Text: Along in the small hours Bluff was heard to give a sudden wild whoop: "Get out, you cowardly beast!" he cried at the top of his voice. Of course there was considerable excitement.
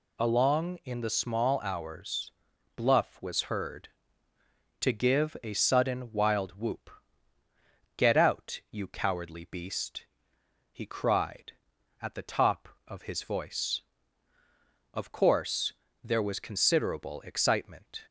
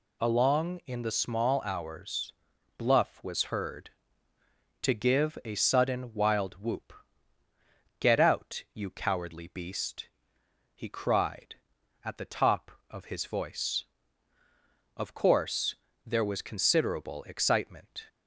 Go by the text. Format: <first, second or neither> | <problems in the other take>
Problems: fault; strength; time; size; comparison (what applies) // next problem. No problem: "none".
neither | pauses between "hours" and "Bluff"; the same in both // pauses between "course" and "there"; slight; the same in both